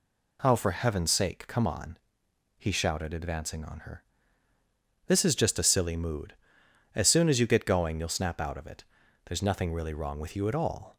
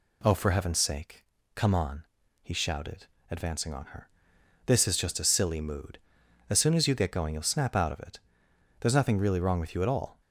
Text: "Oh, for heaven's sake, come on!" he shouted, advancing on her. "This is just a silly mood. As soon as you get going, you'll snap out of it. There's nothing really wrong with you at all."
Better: neither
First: none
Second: none

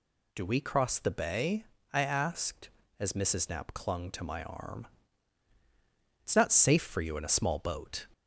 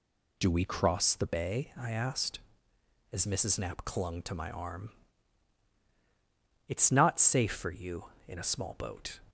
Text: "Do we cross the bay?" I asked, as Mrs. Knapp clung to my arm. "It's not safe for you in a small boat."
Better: neither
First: none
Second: none

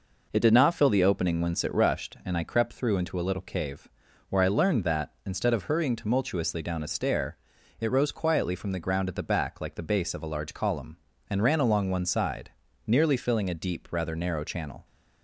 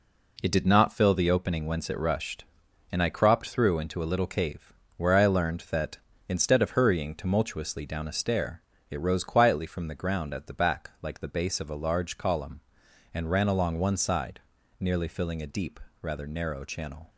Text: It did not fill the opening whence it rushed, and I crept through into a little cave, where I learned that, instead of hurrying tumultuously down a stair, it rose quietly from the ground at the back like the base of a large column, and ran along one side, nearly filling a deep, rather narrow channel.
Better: first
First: none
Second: says "cropped" for "crept"; at 3.0 s

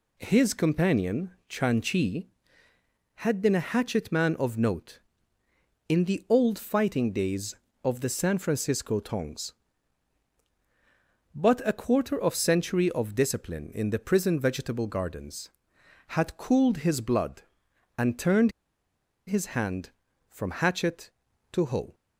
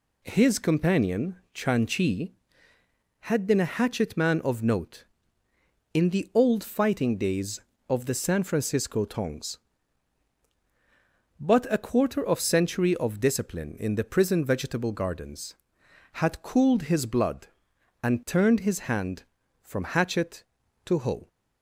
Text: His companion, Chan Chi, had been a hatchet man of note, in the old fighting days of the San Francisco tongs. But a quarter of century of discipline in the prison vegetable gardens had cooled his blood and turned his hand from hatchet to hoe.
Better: second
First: pauses between "turned" and "his"; noticeable; at 18.5 s; 0.75 s long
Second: none

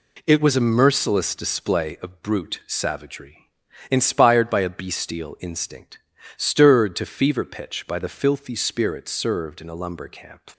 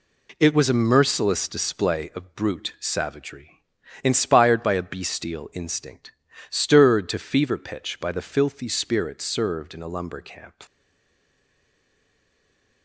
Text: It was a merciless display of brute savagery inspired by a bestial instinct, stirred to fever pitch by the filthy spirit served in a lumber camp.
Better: first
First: pauses between "savagery" and "inspired"; at 3.4 s; 0.42 s long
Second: pauses between "savagery" and "inspired"; at 3.6 s; 0.42 s long // stays silent after the last word; from 10.6 s on; 2.2 s long

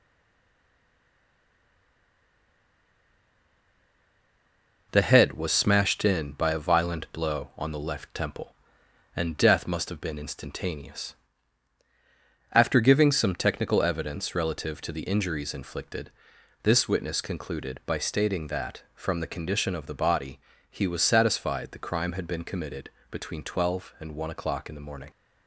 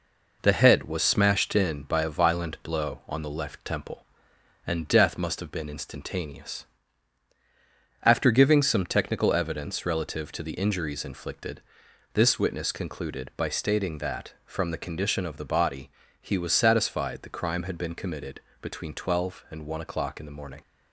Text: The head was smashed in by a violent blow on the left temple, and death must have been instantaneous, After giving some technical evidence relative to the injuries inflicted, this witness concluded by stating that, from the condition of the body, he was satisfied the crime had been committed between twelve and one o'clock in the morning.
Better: second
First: stays silent before the first word; strong; until 4.9 s; 4.9 s long // pauses between "committed" and "between"; slight; at 22.8 s; 0.22 s long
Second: pauses between "committed" and "between"; slight; at 18.3 s; 0.22 s long

